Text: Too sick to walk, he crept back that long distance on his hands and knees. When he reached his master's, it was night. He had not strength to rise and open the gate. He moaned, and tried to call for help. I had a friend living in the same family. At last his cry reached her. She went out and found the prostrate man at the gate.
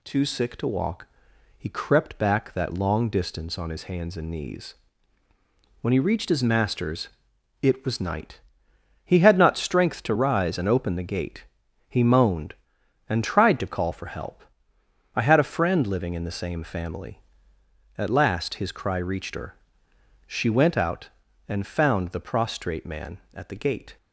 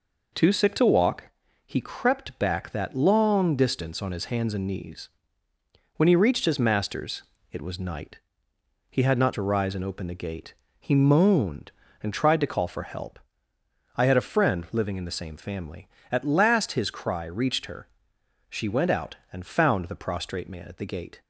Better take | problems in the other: first | skips "strength"; at 9.3 s

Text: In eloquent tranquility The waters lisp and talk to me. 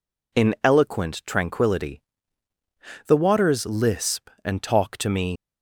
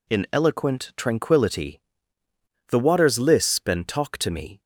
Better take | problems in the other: second | pauses between "tranquility" and "The"; at 2.0 s; 1.0 s long; noticeable in the second // leaves "me" unfinished; at 5.3 s; 85 ms

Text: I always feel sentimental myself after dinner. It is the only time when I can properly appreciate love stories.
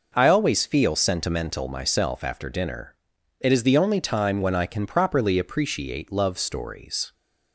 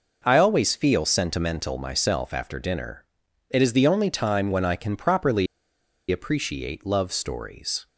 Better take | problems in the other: first | pauses between "properly" and "appreciate"; noticeable; at 5.4 s; 0.65 s long

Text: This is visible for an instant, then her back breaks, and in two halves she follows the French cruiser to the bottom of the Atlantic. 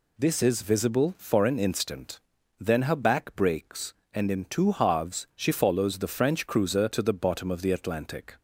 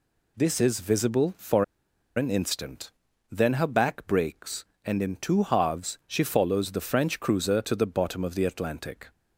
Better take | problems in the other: first | pauses between "for" and "an"; noticeable; at 1.6 s; 0.51 s long

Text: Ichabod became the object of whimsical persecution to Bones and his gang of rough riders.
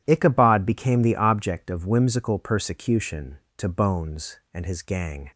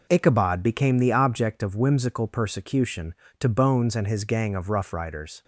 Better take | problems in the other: second | stops before "of rough riders"; at 5.3 s

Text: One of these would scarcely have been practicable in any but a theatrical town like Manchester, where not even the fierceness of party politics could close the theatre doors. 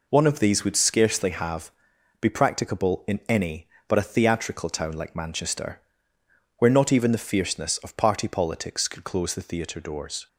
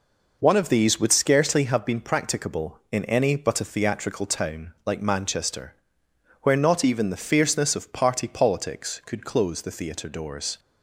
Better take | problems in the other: second | says "be" for "been"; at 2.1 s

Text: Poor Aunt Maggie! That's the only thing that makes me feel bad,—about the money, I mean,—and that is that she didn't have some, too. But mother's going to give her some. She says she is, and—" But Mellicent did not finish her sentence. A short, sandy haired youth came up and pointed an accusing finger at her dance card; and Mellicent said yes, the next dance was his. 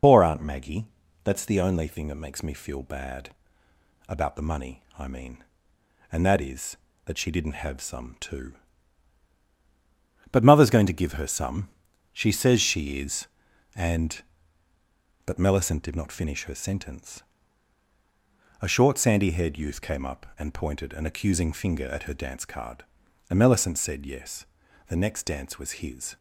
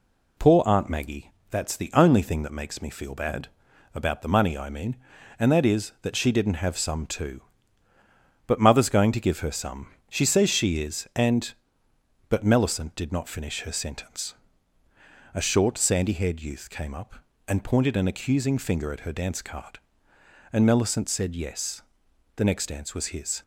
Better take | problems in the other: second | loses the start of "Poor"; at 0.0 s; 65 ms

